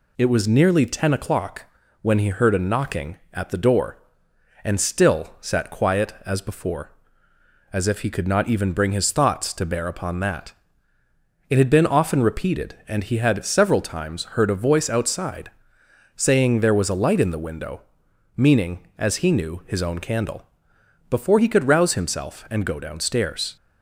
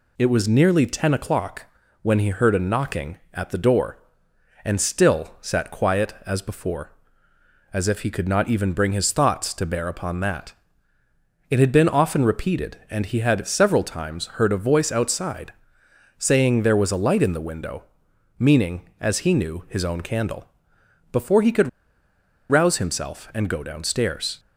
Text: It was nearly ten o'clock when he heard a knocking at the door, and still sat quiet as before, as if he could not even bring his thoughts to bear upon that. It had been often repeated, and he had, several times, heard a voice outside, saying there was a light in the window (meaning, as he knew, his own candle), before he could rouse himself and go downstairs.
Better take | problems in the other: first | pauses between "o'clock" and "when"; slight; at 1.6 s; 0.36 s long; slight in the first // pauses between "could" and "rouse"; noticeable; at 21.6 s; 0.81 s long

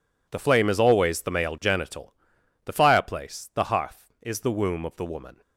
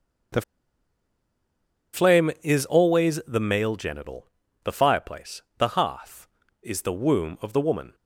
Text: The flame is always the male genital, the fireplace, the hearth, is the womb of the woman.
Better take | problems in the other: first | starts louder than the rest; until 2.9 s; 6.5 dB // pauses between "The" and "flame"; strong; at 0.4 s; 1.5 s long

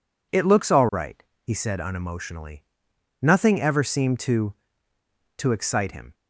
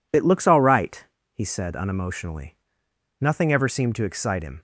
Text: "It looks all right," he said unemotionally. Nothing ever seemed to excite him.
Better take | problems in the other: second | says "to" twice; at 5.3 s

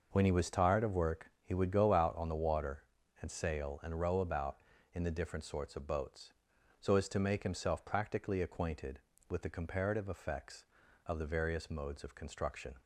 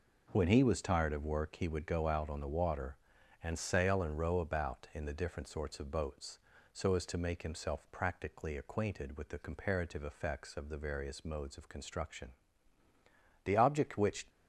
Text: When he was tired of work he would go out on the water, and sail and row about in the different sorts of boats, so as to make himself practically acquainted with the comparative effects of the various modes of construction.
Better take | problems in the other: first | goes on to say "The object which"; noticeable; from 13.4 s on; 0.84 s long

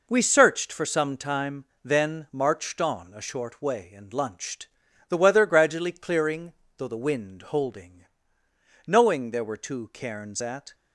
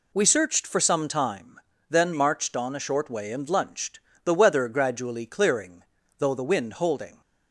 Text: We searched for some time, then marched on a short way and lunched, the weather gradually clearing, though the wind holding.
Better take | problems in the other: second | goes on to say "Knowing there were two cairns at"; strong; from 8.8 s on; 1.8 s long

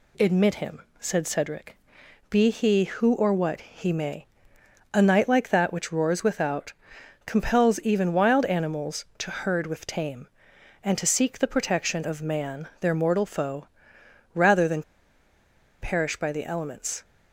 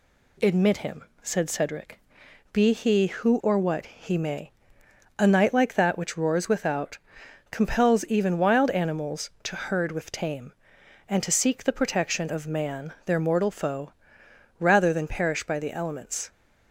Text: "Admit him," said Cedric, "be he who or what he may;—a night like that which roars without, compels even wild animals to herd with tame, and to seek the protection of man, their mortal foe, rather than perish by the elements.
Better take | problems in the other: second | pauses between "than" and "perish"; at 14.8 s; 1.0 s long

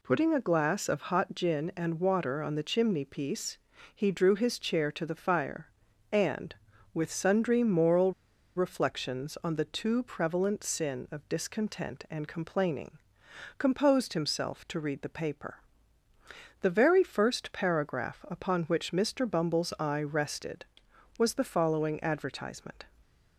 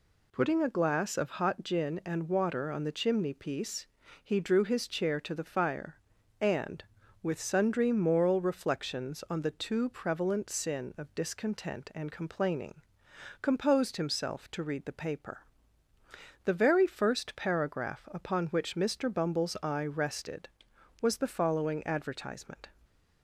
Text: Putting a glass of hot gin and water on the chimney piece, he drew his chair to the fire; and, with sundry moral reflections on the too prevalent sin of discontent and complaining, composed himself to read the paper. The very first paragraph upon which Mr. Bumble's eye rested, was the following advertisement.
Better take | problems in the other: second | pauses between "moral" and "reflections"; at 8.1 s; 0.45 s long

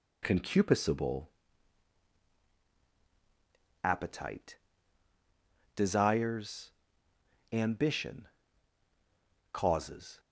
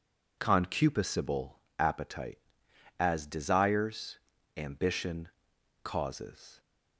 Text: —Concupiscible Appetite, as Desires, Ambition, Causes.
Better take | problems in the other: second | pauses between "Concupiscible" and "Appetite"; strong; at 1.2 s; 2.5 s long; slight in the second // skips "as"; at 5.1 s

